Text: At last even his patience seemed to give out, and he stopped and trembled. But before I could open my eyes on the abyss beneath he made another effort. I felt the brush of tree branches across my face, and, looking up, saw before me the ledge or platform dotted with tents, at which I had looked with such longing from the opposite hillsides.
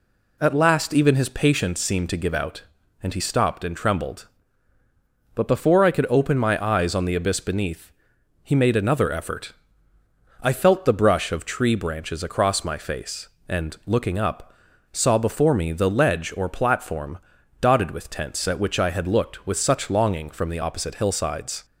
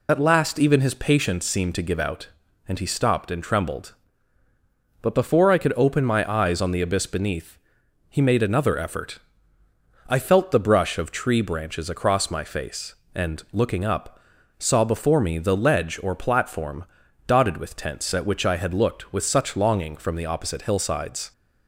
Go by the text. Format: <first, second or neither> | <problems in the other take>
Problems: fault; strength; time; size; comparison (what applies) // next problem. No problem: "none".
first | loses the start of "At"; at 0.0 s; 40 ms // pauses between "beneath" and "he"; noticeable; at 7.5 s; 0.50 s long; noticeable in the first // pauses between "platform" and "dotted"; at 16.8 s; 0.42 s long; also in the first